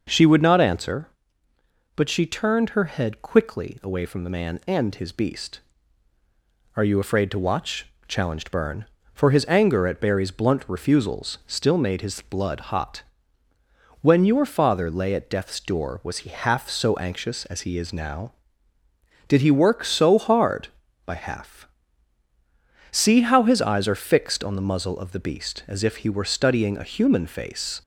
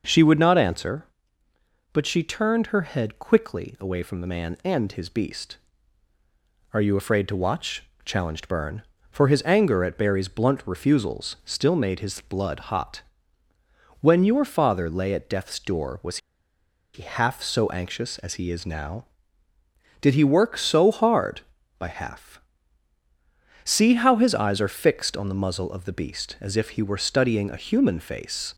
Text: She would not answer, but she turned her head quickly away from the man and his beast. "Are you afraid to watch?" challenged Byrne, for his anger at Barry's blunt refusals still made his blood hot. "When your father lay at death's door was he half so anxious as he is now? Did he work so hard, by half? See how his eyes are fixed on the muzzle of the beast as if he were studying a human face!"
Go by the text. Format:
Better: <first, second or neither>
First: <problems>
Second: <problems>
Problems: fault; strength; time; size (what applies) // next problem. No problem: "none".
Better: first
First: none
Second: pauses between "was" and "he"; noticeable; at 16.1 s; 0.76 s long